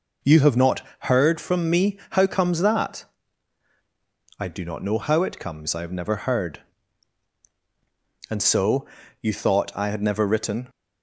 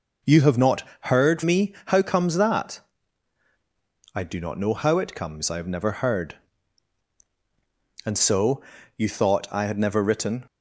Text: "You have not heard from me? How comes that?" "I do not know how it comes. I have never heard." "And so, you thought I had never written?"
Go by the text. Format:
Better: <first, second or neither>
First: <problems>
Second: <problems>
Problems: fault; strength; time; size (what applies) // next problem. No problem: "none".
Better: first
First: pauses between "not" and "heard"; slight; at 0.8 s; 0.18 s long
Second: pauses between "not" and "heard"; slight; at 0.8 s; 0.18 s long // skips "from"; at 1.4 s